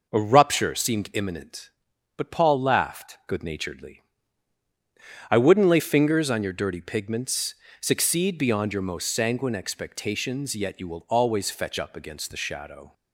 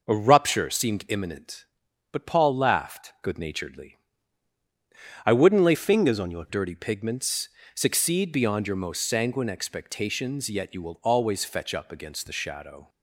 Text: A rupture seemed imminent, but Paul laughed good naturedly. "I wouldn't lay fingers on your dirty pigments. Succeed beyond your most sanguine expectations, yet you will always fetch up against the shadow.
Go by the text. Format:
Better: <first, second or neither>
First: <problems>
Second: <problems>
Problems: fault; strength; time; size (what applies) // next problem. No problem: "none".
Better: first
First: none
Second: changes voice from "fingers" to "your"; from 5.7 to 6.4 s; 0.7 s long